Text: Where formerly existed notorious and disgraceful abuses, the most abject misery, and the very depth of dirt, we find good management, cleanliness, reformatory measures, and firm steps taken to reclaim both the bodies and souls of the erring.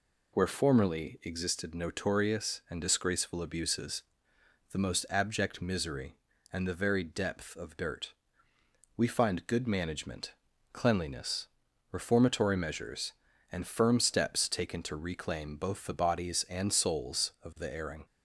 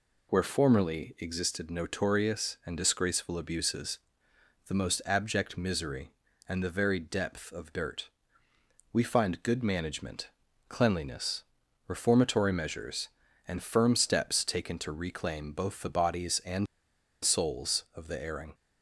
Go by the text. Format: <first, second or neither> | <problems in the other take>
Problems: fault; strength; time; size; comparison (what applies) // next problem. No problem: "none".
first | pauses between "and" and "souls"; noticeable; at 16.6 s; 0.58 s long